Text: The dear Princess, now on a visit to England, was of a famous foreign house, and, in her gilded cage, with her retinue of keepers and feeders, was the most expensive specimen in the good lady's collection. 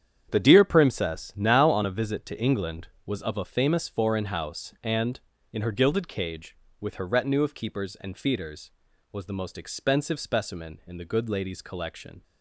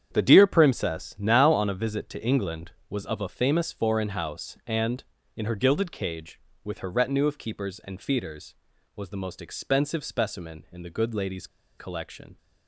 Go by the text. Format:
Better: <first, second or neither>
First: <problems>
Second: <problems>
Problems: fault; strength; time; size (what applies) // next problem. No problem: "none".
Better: first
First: starts louder than the rest; strong; until 1.3 s; 8.5 dB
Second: starts louder than the rest; strong; until 1.1 s; 8.5 dB // pauses between "lady's" and "collection"; slight; at 11.4 s; 0.31 s long